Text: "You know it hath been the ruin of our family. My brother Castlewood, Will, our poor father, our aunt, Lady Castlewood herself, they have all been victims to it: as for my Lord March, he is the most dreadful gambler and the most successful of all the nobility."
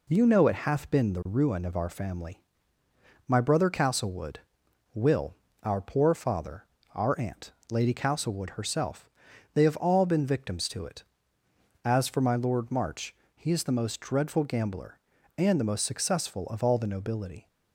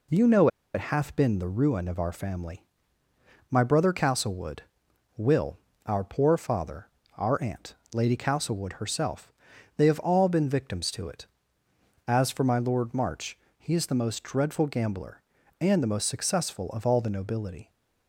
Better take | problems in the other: first | pauses between "know" and "it"; slight; at 0.4 s; 0.27 s long

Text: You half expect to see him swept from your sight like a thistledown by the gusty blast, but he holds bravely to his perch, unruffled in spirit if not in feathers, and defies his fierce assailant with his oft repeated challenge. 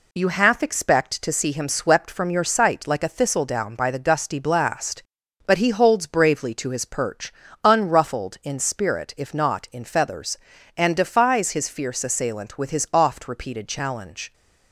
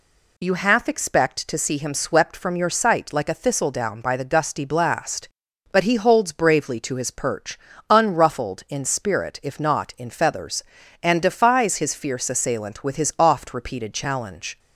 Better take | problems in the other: second | gets quieter; noticeable; throughout; 4 dB

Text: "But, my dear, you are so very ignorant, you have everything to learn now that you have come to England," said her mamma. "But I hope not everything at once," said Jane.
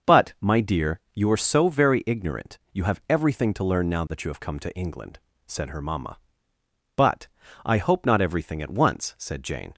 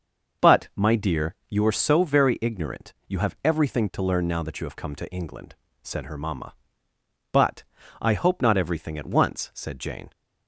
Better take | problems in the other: neither | pauses between "But" and "I"; slight; the same in both

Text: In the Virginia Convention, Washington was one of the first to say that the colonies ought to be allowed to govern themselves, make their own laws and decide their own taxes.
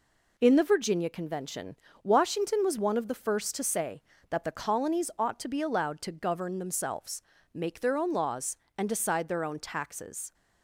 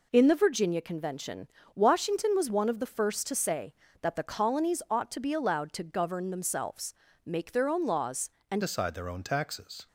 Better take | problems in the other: first | changes voice at "decide"; from 8.6 s on; 1.2 s long

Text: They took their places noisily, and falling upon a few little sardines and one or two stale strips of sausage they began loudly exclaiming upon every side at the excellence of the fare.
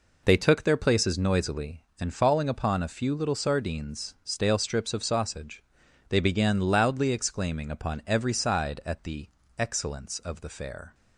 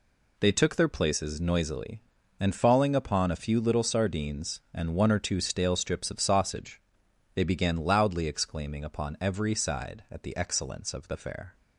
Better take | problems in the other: second | skips "and one or two"; at 4.1 s // pauses between "sausage" and "they"; noticeable; at 5.6 s; 0.46 s long; noticeable in the second // pauses between "the" and "excellence"; slight; at 9.2 s; 0.30 s long

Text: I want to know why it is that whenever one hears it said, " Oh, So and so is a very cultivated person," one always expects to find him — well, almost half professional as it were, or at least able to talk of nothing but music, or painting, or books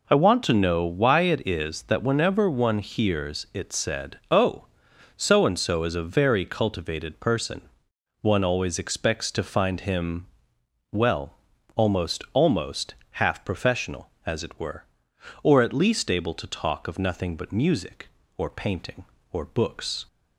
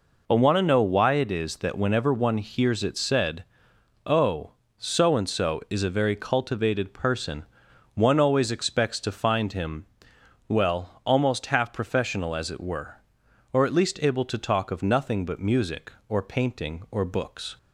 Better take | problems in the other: second | says "almost" twice; at 12.3 s

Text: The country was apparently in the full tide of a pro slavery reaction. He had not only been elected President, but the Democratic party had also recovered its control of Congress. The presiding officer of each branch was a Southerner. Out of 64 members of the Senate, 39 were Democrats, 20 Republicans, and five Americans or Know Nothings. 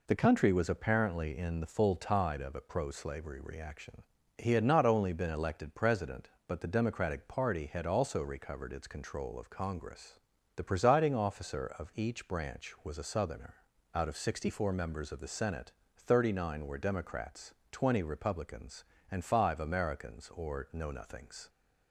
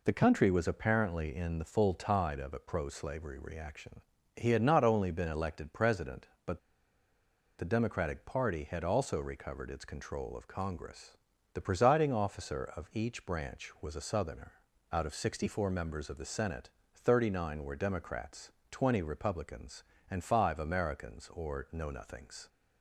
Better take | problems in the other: first | pauses between "but" and "the"; at 6.5 s; 0.99 s long

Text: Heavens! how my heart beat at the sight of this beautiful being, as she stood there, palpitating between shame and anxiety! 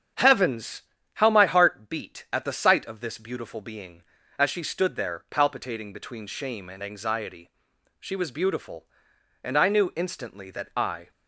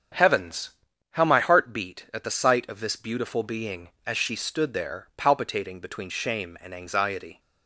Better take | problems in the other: second | starts louder than the rest; strong; until 1.4 s; 8 dB; strong in the second // goes on to say "She was beautiful and I knew instantly that I"; strong; from 7.9 s on; 3.1 s long

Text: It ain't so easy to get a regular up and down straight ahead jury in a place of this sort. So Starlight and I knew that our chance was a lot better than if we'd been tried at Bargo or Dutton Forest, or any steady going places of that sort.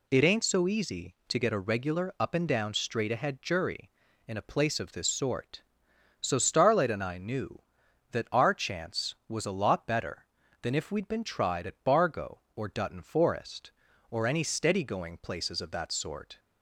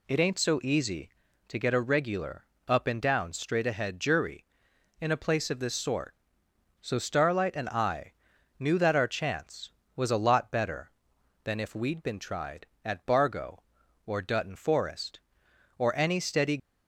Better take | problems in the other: first | pauses between "regular" and "up"; slight; at 2.4 s; 0.24 s long // pauses between "I" and "knew"; noticeable; at 8.1 s; 0.46 s long // stops before "going places of that sort"; at 16.5 s

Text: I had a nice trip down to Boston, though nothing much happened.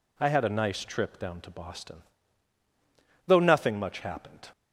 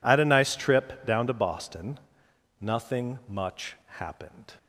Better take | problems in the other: first | skips "though"; at 2.2 s

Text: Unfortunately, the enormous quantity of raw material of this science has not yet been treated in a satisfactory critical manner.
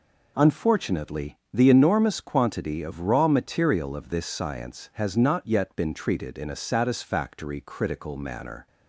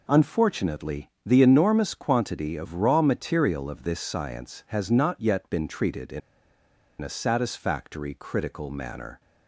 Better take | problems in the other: first | pauses between "in" and "a"; noticeable; at 6.2 s; 0.81 s long

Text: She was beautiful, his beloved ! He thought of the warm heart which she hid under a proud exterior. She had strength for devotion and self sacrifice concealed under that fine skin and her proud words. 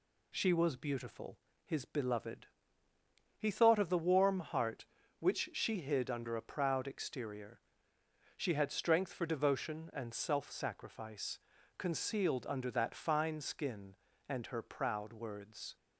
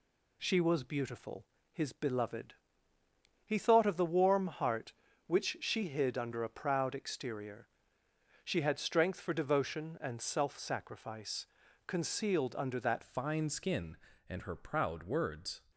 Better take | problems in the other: first | pauses between "sacrifice" and "concealed"; at 11.4 s; 0.40 s long; also in the first // changes voice at "fine"; from 13.0 s on; 2.6 s long

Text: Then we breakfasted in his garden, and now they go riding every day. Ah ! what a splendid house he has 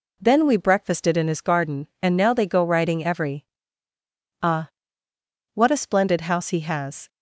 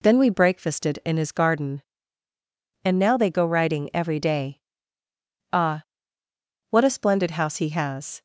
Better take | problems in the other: second | skips "day"; at 3.9 s

